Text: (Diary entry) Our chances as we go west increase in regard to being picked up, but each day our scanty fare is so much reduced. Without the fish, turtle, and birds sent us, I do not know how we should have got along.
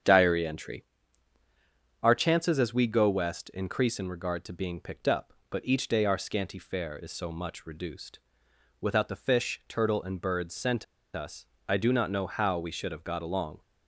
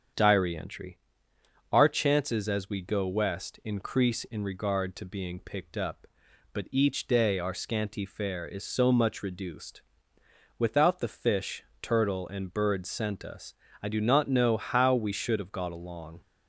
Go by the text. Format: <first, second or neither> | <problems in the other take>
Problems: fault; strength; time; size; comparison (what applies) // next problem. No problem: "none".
second | starts louder than the rest; strong; until 2.2 s; 8.5 dB; strong in the second // pauses between "sent" and "us"; slight; at 10.8 s; 0.29 s long